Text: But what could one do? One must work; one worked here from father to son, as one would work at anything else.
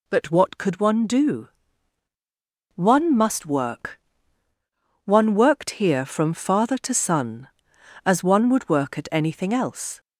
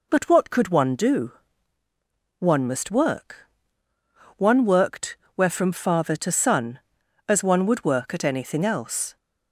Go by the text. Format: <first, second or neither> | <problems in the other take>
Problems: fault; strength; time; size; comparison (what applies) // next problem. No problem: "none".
first | says "where" for "here"; at 5.3 s